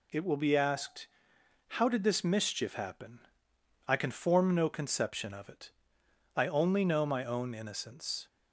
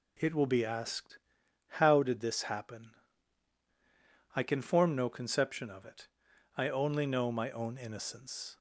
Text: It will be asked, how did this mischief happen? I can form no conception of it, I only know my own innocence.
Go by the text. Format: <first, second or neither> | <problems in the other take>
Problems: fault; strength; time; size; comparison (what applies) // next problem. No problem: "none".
first | skips "mischief"; at 2.4 s